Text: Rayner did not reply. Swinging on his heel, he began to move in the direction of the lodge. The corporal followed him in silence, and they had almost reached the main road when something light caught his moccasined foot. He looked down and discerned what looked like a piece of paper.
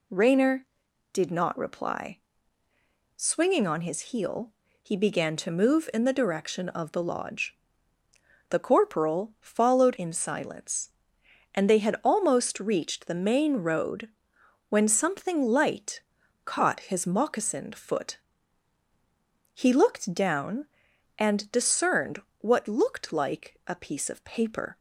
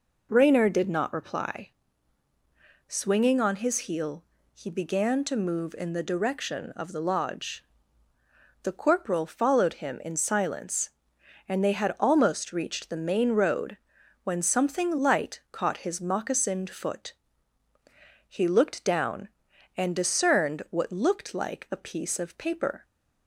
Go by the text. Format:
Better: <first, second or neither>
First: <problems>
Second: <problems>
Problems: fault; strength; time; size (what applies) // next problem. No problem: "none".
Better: second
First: skips "him"; at 9.9 s // pauses between "road" and "when"; noticeable; at 14.0 s; 0.60 s long // pauses between "light" and "caught"; at 16.0 s; 0.44 s long // pauses between "discerned" and "what"; slight; at 22.2 s; 0.18 s long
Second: pauses between "road" and "when"; noticeable; at 13.7 s; 0.46 s long